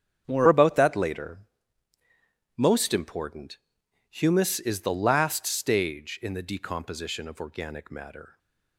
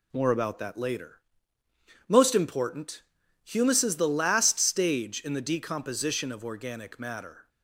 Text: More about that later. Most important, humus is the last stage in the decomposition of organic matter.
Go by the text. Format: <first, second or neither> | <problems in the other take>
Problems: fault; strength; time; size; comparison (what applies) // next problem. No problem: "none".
second | starts louder than the rest; strong; until 1.3 s; 7.5 dB // changes voice at "about"; from 0.4 s on; 7.9 s long